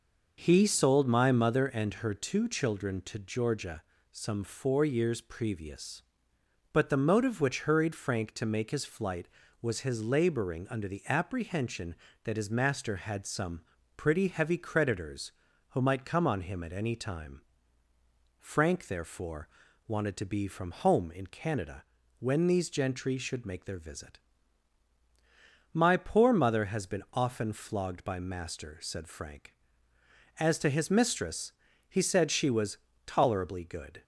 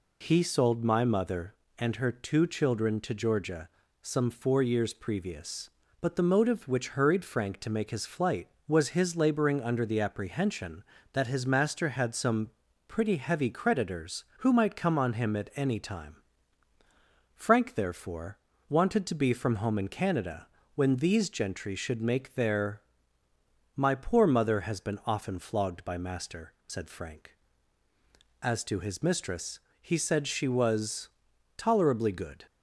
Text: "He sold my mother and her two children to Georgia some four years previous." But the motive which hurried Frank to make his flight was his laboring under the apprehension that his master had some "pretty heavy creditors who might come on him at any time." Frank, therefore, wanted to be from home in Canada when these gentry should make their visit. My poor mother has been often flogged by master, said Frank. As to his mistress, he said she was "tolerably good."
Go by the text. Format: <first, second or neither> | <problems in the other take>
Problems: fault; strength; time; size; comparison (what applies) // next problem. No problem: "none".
first | pauses between "Georgia" and "some"; slight; at 3.6 s; 0.36 s long; slight in the first // pauses between "some" and "pretty"; slight; at 12.5 s; 0.34 s long; slight in the first // pauses between "Canada" and "when"; slight; at 20.4 s; 0.30 s long; slight in the first // skips "visit"; at 23.2 s // pauses between "was" and "tolerably"; noticeable; at 31.0 s; 0.48 s long; slight in the first